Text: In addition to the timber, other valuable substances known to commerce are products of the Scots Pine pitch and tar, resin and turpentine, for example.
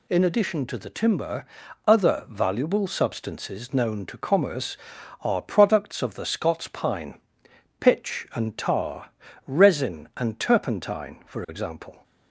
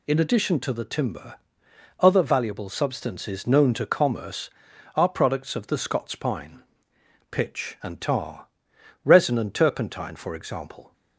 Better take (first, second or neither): neither